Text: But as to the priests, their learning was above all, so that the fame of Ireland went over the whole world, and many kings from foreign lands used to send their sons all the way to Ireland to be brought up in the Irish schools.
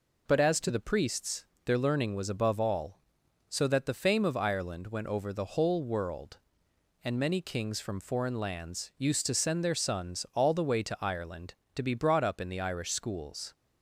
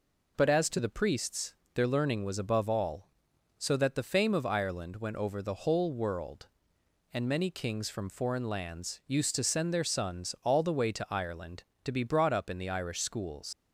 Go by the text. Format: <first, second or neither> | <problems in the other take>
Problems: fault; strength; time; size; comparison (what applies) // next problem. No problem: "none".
first | leaves "schools" unfinished; at 13.5 s; 120 ms